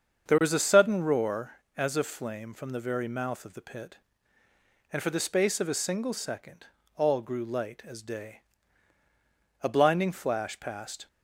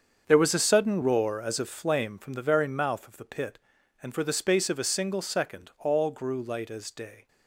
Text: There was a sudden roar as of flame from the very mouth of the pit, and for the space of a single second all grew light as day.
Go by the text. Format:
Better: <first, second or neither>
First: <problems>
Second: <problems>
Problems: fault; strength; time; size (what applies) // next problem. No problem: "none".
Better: second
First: starts louder than the rest; until 1.3 s; 7 dB // pauses between "second" and "all"; slight; at 6.6 s; 0.30 s long // goes on to say "A blinding flash passed"; from 9.6 s on; 1.4 s long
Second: starts louder than the rest; until 1.2 s; 7 dB